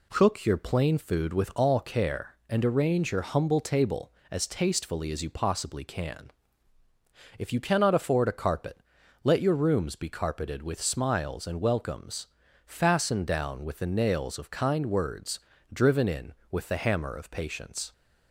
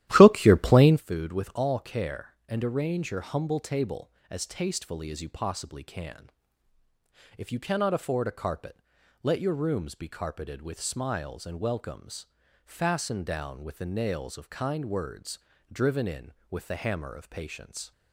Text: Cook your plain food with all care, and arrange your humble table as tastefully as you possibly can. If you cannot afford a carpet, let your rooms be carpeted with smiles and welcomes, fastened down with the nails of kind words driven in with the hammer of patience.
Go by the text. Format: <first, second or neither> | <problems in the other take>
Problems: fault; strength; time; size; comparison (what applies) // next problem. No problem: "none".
first | starts louder than the rest; strong; until 1.0 s; 13.5 dB // pauses between "words" and "driven"; slight; at 15.3 s; 0.32 s long; slight in the first